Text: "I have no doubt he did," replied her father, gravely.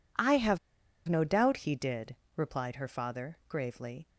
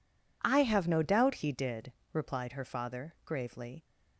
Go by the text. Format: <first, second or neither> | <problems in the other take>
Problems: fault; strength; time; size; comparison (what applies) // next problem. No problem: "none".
second | pauses between "have" and "no"; noticeable; at 0.5 s; 0.49 s long